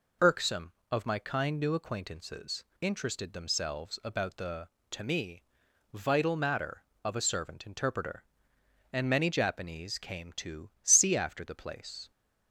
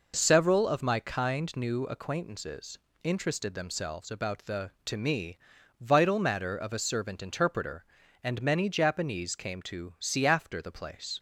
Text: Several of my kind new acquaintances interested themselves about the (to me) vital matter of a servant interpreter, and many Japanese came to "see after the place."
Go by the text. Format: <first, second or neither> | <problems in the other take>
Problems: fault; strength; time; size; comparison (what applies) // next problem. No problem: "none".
second | says "Irksome" for "Several"; at 0.2 s // pauses between "acquaintances" and "interested"; slight; at 2.6 s; 0.16 s long; slight in the second // pauses between "to" and "see"; slight; at 10.6 s; 0.16 s long